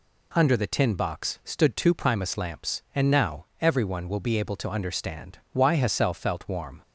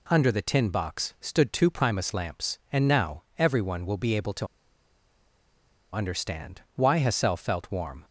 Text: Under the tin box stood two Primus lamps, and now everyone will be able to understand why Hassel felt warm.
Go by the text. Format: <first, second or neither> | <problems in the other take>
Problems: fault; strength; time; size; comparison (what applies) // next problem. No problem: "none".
first | pauses between "to" and "understand"; strong; at 4.4 s; 1.4 s long